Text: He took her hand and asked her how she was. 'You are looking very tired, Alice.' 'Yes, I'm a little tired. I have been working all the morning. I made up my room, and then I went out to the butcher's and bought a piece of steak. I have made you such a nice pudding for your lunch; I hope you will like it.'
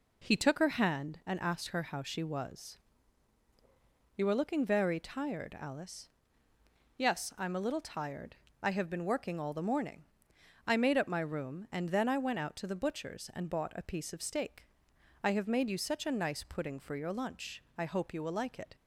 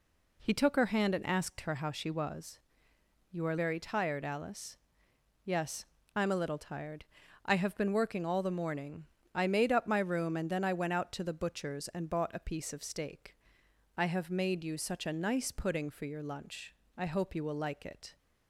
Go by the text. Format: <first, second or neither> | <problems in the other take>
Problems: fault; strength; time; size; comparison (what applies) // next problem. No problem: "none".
first | skips "looking"; at 3.5 s